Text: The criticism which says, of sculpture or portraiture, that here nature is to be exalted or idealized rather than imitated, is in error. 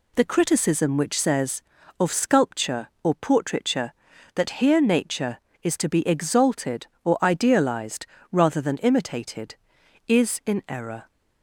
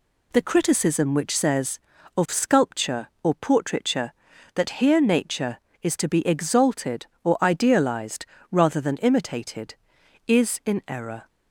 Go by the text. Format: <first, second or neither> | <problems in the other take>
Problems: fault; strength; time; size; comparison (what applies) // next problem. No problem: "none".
neither | pauses between "idealized" and "rather"; slight; the same in both